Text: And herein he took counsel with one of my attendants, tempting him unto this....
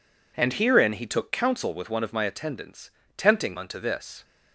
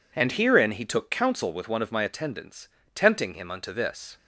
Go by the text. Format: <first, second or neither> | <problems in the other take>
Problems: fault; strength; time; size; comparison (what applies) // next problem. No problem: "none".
second | skips "him"; at 3.5 s